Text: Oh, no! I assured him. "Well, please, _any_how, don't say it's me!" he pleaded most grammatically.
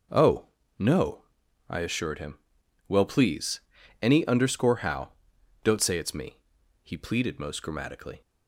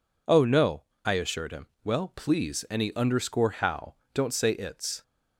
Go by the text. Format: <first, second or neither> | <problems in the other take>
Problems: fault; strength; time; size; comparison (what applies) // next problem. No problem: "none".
first | stops before "me he pleaded most grammatically"; at 5.0 s